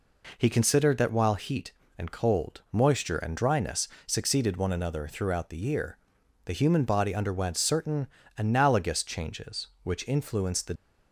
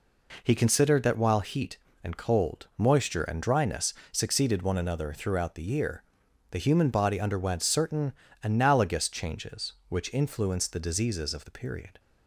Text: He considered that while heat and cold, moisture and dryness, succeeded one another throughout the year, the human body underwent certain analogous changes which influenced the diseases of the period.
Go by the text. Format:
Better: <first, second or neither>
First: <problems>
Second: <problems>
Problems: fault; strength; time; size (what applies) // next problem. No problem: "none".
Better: second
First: pauses between "certain" and "analogous"; slight; at 8.0 s; 0.30 s long // stops before "diseases of the period"; at 10.7 s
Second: pauses between "certain" and "analogous"; slight; at 8.1 s; 0.30 s long